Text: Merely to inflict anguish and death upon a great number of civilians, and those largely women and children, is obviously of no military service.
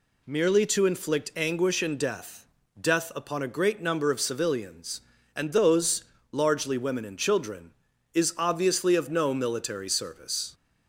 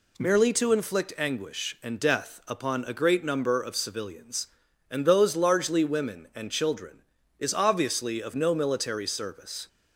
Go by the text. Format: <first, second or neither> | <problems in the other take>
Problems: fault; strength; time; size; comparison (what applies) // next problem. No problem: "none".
second | says "death" twice; at 2.7 s // pauses between "those" and "largely"; slight; at 6.0 s; 0.26 s long